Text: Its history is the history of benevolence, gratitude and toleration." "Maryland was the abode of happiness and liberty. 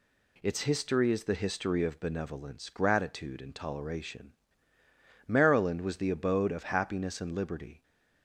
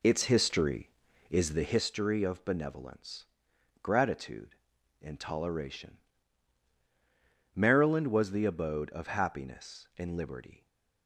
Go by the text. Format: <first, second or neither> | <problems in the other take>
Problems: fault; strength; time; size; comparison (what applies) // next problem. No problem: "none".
first | starts louder than the rest; slight; until 1.9 s; 3.5 dB